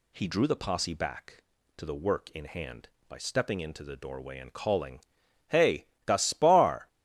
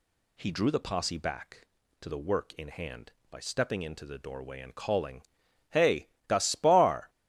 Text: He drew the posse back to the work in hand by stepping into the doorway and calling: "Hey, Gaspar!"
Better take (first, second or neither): neither